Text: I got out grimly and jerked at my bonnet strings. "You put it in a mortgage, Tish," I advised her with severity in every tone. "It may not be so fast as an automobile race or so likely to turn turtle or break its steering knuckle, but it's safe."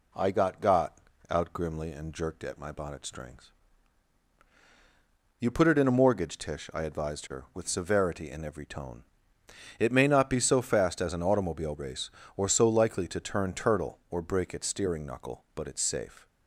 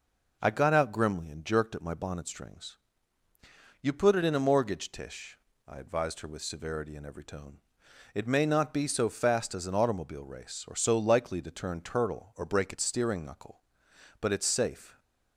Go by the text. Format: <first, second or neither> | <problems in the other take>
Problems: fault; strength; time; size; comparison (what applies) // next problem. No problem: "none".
second | says "got" twice; at 0.6 s